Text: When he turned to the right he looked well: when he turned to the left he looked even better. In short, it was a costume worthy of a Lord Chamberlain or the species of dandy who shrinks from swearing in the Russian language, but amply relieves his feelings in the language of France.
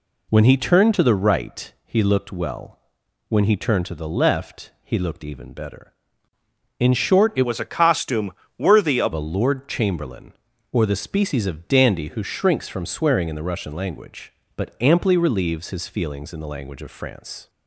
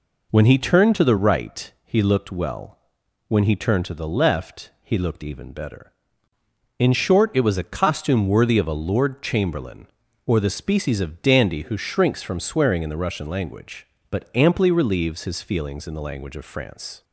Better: second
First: changes voice from "was" to "of"; from 7.4 to 9.1 s; 1.7 s long // pauses between "costume" and "worthy"; slight; at 8.3 s; 0.26 s long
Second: none

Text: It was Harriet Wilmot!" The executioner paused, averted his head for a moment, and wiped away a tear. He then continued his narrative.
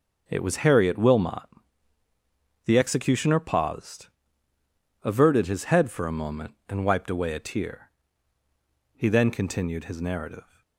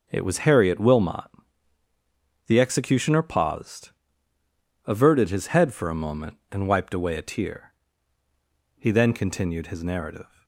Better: neither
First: starts louder than the rest; noticeable; until 1.3 s; 6 dB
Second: starts louder than the rest; until 1.1 s; 6 dB

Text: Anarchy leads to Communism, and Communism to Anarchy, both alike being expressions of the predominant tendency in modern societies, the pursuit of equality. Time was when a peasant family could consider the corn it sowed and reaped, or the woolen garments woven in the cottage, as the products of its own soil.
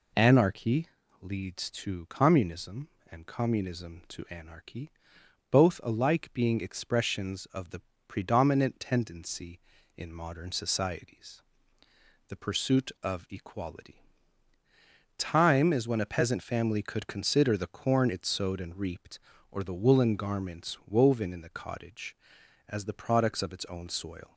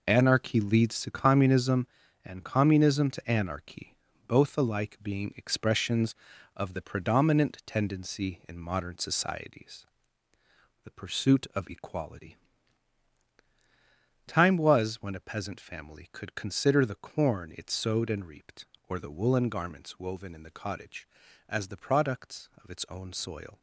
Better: second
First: pauses between "Anarchy" and "leads"; at 0.8 s; 0.38 s long // pauses between "the" and "predominant"; slight; at 7.8 s; 0.26 s long // says "is" for "was"; at 15.7 s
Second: none

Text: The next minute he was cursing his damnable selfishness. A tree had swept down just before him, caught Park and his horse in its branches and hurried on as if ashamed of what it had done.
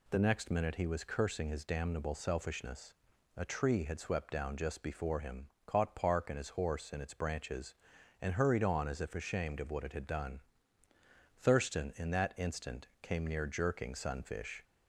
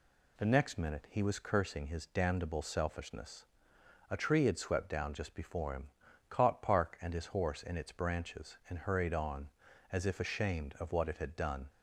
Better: second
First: goes on to say "Thurston in that instant came near jerking Sunfish"; strong; from 11.3 s on; 3.2 s long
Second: none

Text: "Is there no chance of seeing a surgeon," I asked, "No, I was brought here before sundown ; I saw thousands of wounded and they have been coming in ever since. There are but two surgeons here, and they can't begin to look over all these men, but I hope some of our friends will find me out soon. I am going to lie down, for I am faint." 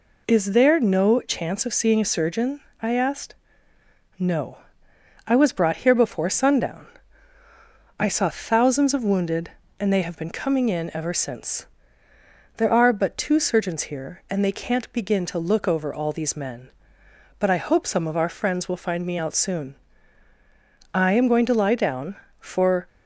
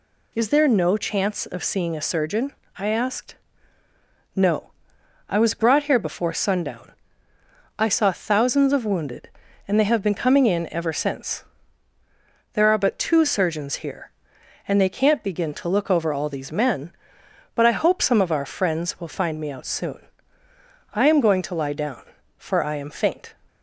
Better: second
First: stops before "I am faint"; at 22.8 s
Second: none

